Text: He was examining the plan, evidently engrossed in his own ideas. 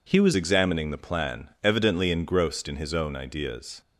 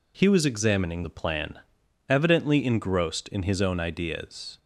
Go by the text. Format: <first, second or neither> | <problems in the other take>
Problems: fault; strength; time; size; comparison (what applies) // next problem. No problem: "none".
second | changes voice at "examining"; from 0.3 s on; 3.5 s long